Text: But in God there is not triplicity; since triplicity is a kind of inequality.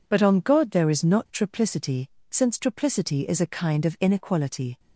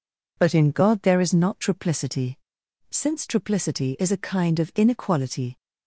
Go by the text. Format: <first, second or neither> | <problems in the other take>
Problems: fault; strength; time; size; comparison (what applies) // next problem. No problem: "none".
second | says "on" for "in"; at 0.2 s